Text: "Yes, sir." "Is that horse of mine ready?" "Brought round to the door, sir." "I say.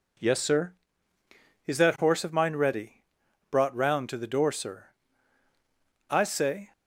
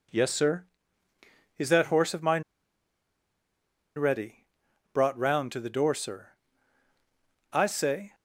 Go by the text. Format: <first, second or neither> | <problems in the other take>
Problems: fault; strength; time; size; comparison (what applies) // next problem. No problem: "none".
first | pauses between "mine" and "ready"; strong; at 2.4 s; 1.5 s long